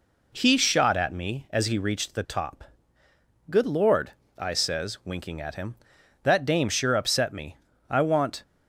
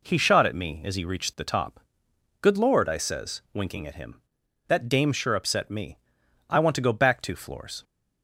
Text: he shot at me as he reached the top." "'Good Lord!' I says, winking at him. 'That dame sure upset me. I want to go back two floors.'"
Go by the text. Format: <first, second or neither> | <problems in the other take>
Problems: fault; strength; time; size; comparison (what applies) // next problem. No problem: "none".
second | stops before "to go back two floors"; at 8.4 s